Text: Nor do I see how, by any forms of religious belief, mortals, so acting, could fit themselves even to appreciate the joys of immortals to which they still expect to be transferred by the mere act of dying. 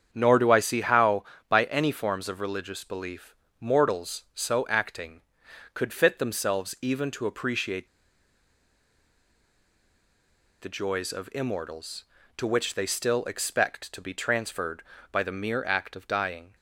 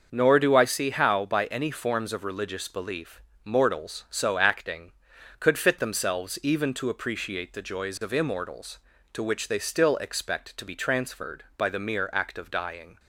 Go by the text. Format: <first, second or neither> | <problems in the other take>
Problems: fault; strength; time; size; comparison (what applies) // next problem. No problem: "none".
second | starts louder than the rest; strong; until 1.1 s; 8 dB; also in the second // pauses between "appreciate" and "the"; strong; at 7.8 s; 2.7 s long